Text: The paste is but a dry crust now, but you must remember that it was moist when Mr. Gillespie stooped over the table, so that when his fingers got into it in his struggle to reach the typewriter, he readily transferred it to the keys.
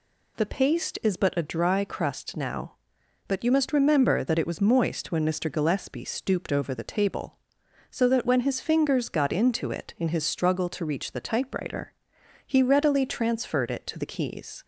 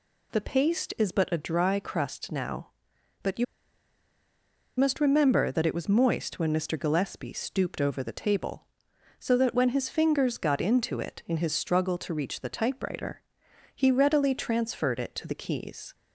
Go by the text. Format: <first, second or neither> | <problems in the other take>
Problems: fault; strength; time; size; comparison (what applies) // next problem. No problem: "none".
first | pauses between "you" and "must"; strong; at 3.4 s; 1.3 s long